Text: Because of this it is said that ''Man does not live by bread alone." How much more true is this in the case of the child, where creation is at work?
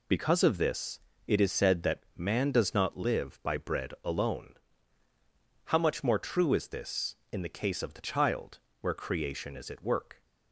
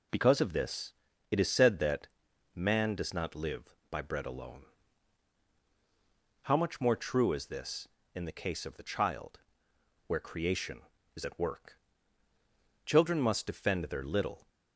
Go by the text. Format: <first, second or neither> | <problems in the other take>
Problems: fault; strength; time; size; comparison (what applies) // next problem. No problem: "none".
first | pauses between "this" and "it"; slight; at 0.9 s; 0.36 s long; slight in the first // pauses between "that" and "Man"; noticeable; at 2.0 s; 0.48 s long // goes on to say "Children must defend their little"; from 12.8 s on; 1.6 s long